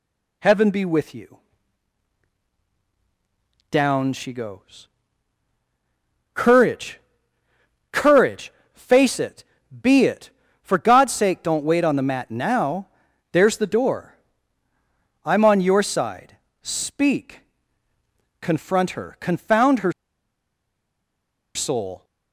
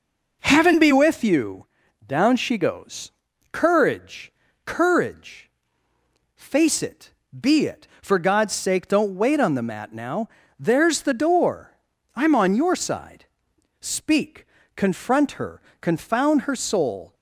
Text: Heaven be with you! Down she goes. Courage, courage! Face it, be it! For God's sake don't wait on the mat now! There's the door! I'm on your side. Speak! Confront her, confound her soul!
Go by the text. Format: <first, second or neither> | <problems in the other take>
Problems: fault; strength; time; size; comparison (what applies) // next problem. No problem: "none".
second | pauses between "her" and "soul"; strong; at 19.9 s; 1.6 s long